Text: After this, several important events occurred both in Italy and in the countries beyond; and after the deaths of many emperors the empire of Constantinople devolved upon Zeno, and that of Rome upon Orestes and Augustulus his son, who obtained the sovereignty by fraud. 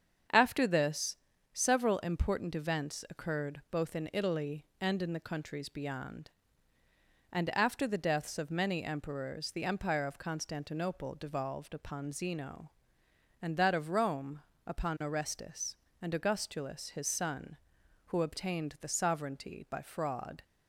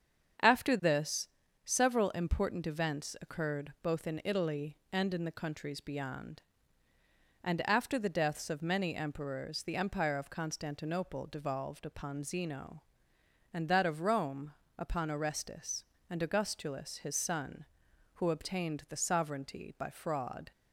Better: neither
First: starts louder than the rest; strong; until 1.7 s; 7.5 dB // pauses between "Rome" and "upon"; slight; at 14.4 s; 0.24 s long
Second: starts louder than the rest; strong; until 1.8 s; 7.5 dB // pauses between "Rome" and "upon"; slight; at 14.5 s; 0.24 s long

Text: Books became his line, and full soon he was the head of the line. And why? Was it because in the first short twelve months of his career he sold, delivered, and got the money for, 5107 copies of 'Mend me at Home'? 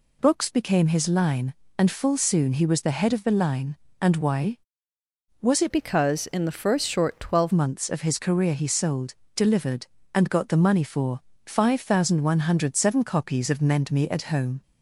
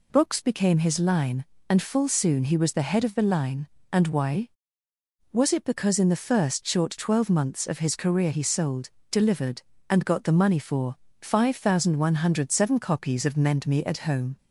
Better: second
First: changes voice from "because" to "twelve"; from 5.7 to 7.5 s; 1.8 s long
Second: none

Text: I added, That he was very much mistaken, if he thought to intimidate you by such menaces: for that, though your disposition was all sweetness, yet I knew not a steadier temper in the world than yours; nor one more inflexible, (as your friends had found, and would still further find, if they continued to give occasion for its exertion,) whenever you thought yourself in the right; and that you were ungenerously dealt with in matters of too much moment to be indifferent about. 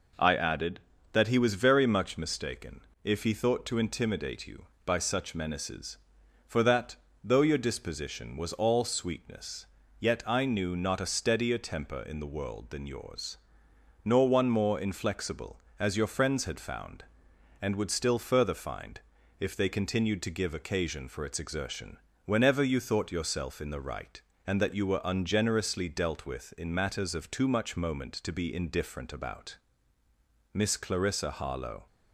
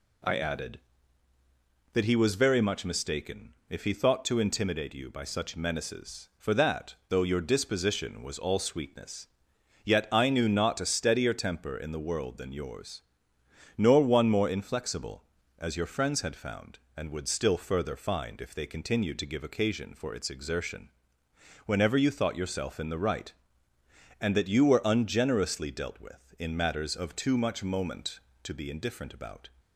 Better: second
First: goes on to say "Miss Clarissa Harlowe"; from 30.5 s on; 1.3 s long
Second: none

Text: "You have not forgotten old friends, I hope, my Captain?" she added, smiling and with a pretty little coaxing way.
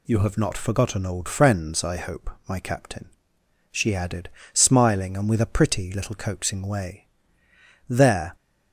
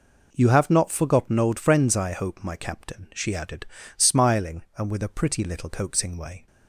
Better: second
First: goes on to say "There"; slight; from 7.8 s on; 0.46 s long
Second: none

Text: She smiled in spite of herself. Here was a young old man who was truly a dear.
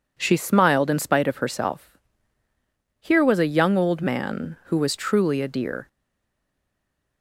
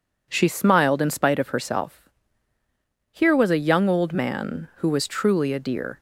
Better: second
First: stays silent after the last word; noticeable; from 5.8 s on; 1.4 s long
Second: none

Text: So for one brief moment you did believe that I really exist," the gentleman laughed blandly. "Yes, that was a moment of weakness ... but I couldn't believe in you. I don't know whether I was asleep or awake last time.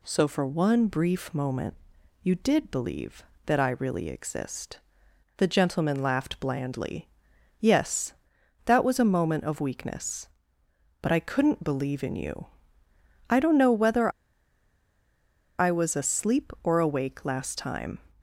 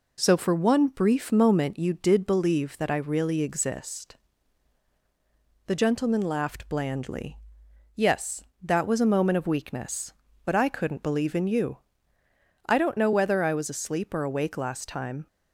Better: second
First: pauses between "moment" and "you"; noticeable; at 1.7 s; 0.48 s long // pauses between "whether" and "I"; strong; at 14.1 s; 1.4 s long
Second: none

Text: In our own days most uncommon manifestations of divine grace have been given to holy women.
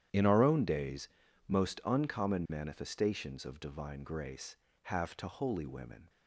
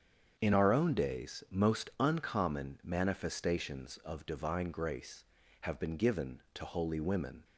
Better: second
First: starts louder than the rest; strong; until 1.5 s; 10 dB // pauses between "days" and "most"; at 1.0 s; 0.38 s long // skips "been given"; at 5.1 s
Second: starts louder than the rest; strong; until 1.3 s; 7.5 dB

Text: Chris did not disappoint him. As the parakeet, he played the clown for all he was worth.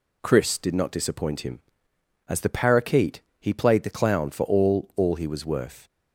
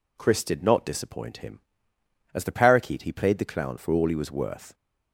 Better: second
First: says "all" twice; at 4.9 s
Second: none

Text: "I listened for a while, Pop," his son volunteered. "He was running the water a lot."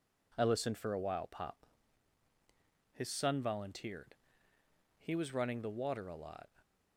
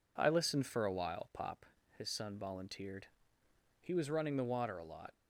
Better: neither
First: none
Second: none

